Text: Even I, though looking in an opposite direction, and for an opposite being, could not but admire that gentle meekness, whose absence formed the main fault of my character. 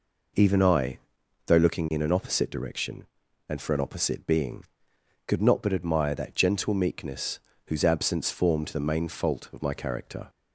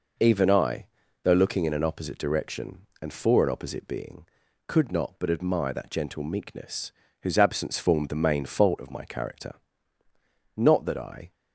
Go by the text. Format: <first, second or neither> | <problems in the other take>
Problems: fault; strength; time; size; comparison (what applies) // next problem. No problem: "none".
first | goes on to say "Not that I"; noticeable; from 10.5 s on; 0.78 s long